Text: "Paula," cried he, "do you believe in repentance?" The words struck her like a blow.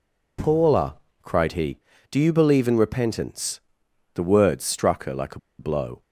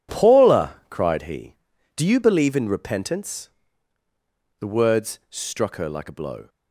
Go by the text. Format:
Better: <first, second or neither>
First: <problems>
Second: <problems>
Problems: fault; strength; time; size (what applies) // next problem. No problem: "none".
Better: second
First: pauses between "a" and "blow"; slight; at 5.3 s; 0.19 s long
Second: none